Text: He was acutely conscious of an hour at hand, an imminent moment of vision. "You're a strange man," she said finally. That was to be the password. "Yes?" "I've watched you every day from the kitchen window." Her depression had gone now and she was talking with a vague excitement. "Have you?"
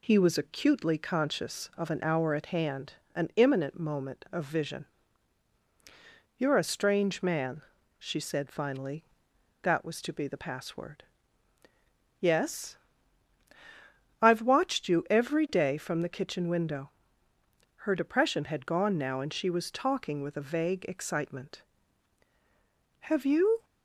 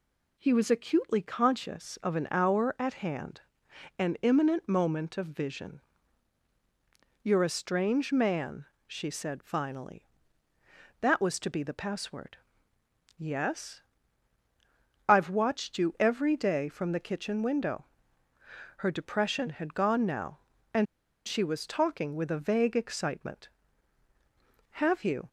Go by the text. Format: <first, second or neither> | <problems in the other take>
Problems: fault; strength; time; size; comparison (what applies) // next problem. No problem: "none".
first | pauses between "and" and "she"; at 20.8 s; 0.42 s long